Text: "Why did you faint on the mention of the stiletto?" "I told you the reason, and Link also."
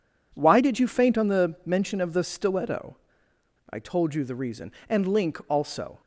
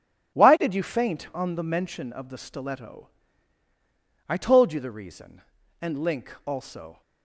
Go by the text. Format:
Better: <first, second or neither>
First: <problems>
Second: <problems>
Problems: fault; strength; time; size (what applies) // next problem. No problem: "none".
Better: neither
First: none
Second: none